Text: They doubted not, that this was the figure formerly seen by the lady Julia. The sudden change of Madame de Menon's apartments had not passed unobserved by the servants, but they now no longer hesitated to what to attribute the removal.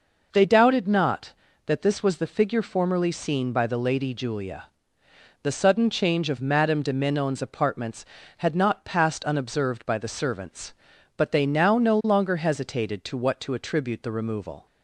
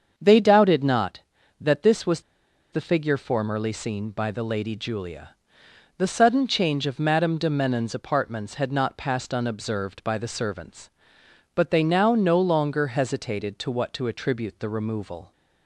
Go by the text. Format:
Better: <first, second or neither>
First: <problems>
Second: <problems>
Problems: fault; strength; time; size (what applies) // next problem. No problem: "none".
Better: first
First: none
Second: starts louder than the rest; until 1.1 s; 7 dB // pauses between "was" and "the"; noticeable; at 2.2 s; 0.50 s long